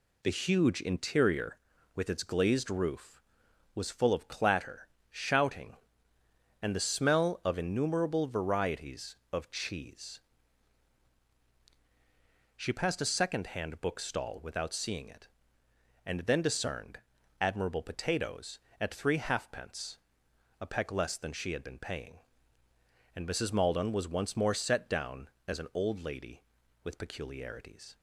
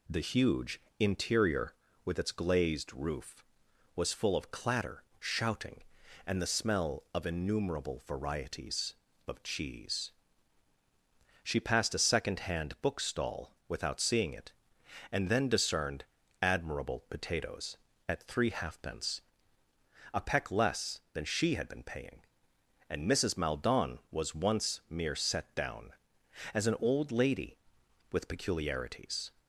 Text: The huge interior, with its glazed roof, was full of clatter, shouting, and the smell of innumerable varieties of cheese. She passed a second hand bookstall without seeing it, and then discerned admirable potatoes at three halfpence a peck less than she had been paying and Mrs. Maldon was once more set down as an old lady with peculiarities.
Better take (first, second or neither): first